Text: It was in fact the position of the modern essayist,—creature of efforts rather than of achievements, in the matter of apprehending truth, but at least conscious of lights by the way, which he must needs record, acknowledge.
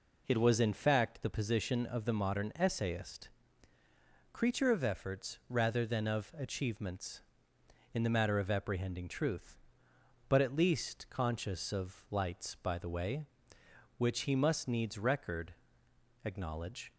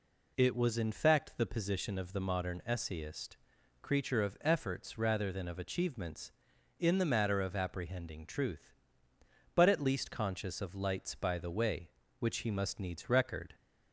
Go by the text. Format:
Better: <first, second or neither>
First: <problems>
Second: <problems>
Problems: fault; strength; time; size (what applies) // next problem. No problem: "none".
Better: first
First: none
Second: stops before "acknowledge"; at 13.5 s